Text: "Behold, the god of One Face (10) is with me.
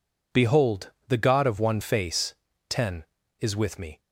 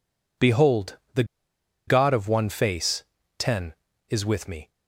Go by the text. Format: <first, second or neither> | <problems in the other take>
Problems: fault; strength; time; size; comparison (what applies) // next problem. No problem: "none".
first | pauses between "the" and "god"; noticeable; at 1.2 s; 0.63 s long